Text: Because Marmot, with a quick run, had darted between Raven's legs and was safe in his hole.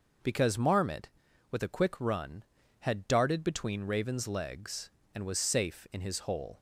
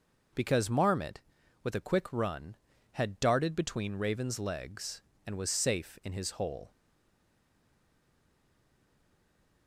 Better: first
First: none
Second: stays silent after the last word; strong; from 6.6 s on; 3.0 s long

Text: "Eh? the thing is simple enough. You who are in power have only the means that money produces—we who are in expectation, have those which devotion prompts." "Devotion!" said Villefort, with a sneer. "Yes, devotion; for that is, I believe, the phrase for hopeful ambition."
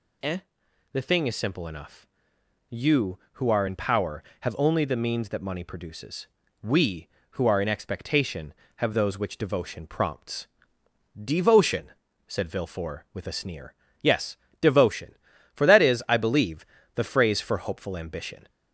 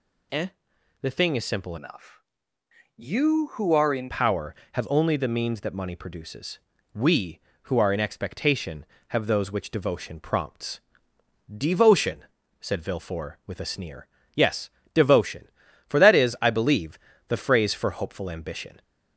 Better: first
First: none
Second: changes voice from "enough" to "in"; from 1.7 to 4.1 s; 2.4 s long

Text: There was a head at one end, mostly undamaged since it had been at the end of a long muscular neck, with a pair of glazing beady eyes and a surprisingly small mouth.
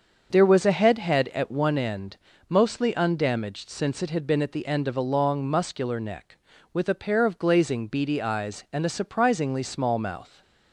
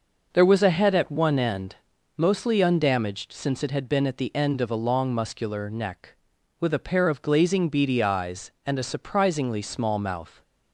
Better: second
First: starts louder than the rest; until 1.3 s; 6.5 dB // says "head" twice; at 0.9 s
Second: none

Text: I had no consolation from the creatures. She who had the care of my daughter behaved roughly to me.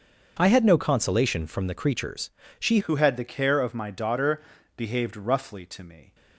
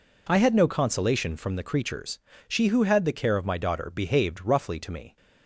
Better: second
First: starts louder than the rest; noticeable; until 1.4 s; 6 dB // changes voice at "who"; from 2.8 s on; 3.3 s long // pauses between "daughter" and "behaved"; slight; at 4.4 s; 0.36 s long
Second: none

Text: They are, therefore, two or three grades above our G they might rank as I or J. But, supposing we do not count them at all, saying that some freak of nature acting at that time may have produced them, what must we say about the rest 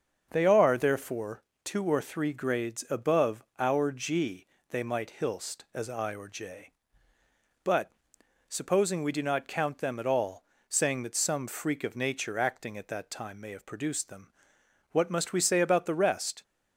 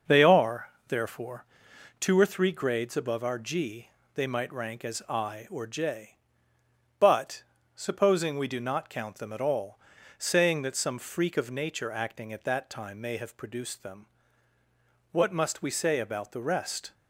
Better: second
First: starts louder than the rest; until 1.3 s; 7 dB // pauses between "above" and "our"; slight; at 3.4 s; 0.16 s long // pauses between "G" and "they"; slight; at 4.4 s; 0.24 s long // says "hilst" for "rank"; at 5.1 s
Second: starts louder than the rest; noticeable; until 1.2 s; 6 dB // pauses between "G" and "they"; slight; at 3.8 s; 0.28 s long

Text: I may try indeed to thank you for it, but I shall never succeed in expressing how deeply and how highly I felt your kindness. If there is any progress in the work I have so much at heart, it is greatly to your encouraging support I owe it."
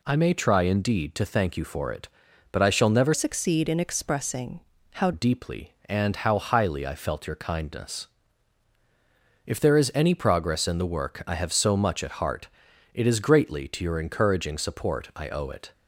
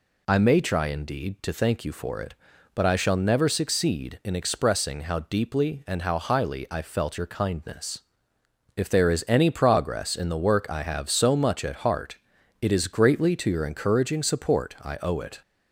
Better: second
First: changes voice from "succeed" to "how"; from 3.1 to 5.1 s; 2.0 s long // pauses between "expressing" and "how"; slight; at 4.6 s; 0.30 s long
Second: none

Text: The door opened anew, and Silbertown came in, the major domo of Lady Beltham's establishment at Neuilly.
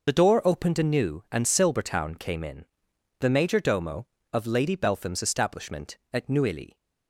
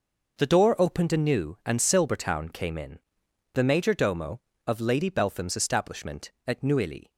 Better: second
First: loses the start of "The"; at 0.0 s; 30 ms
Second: none

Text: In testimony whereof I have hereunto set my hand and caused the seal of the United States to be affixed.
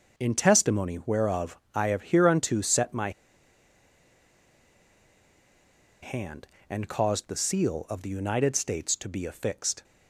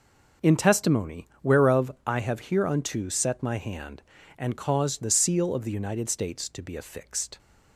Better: second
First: pauses between "whereof" and "I"; slight; at 1.5 s; 0.16 s long // pauses between "my" and "hand"; strong; at 3.0 s; 2.9 s long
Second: pauses between "whereof" and "I"; slight; at 1.8 s; 0.16 s long

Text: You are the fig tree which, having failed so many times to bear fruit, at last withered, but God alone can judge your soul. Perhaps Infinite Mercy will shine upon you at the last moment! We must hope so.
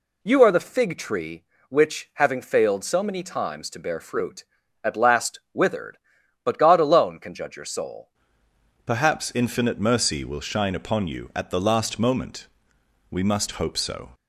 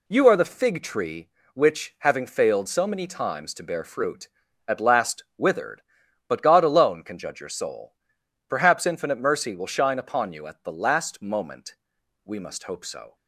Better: second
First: changes voice at "Perhaps"; from 8.8 s on; 5.3 s long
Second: none

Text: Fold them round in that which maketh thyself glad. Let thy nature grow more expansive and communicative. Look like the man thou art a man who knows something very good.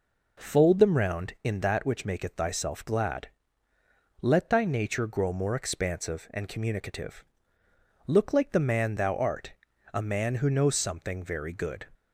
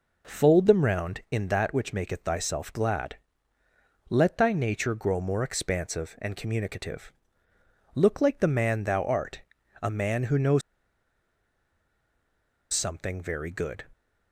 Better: first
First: pauses between "art" and "a"; at 9.5 s; 0.40 s long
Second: pauses between "art" and "a"; at 9.4 s; 0.40 s long // pauses between "knows" and "something"; strong; at 10.6 s; 2.1 s long

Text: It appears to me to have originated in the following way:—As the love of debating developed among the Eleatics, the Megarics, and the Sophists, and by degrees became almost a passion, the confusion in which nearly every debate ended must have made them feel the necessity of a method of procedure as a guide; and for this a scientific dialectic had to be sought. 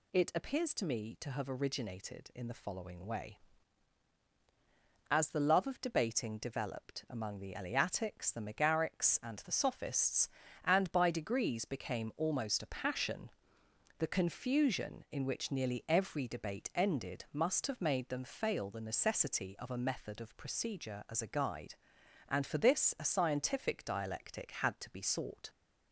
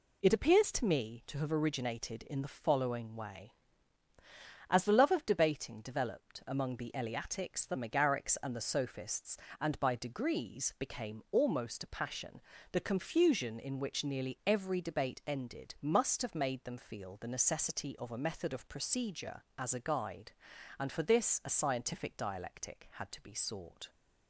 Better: second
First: says "fail" for "feel"; at 18.2 s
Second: none

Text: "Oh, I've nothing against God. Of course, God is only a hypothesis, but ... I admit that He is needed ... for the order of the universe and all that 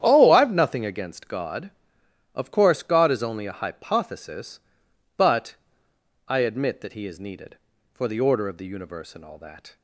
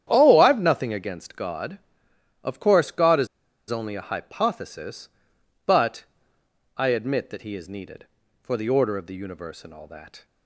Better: first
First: starts louder than the rest; strong; until 1.0 s; 9.5 dB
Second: starts louder than the rest; strong; until 1.0 s; 10 dB // pauses between "is" and "only"; at 3.2 s; 0.43 s long

